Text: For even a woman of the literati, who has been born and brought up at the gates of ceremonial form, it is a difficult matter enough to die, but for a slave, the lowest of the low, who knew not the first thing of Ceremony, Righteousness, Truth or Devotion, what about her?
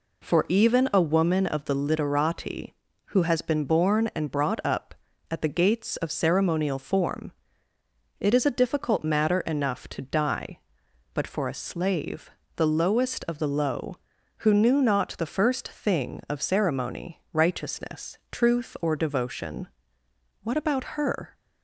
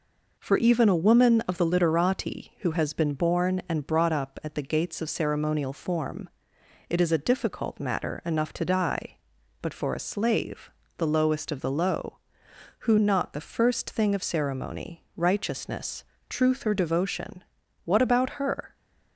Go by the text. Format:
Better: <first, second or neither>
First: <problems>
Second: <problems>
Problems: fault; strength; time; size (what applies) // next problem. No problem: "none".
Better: first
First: none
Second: skips "knew"; at 12.9 s